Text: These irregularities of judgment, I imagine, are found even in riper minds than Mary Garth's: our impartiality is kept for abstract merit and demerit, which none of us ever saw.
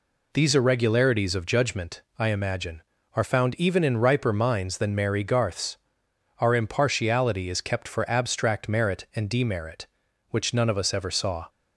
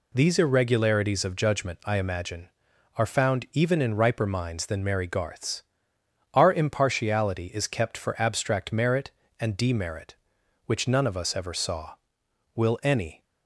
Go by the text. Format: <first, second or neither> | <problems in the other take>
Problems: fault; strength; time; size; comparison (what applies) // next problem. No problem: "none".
first | goes on to say "Will any"; noticeable; from 12.5 s on; 0.70 s long